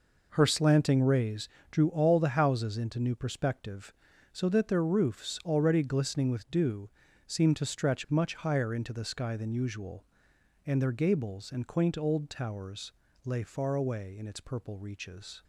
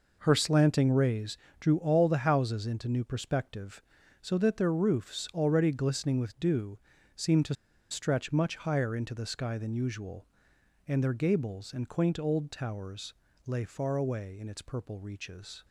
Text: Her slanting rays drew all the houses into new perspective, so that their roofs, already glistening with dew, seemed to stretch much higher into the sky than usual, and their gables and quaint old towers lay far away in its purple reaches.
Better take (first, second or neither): first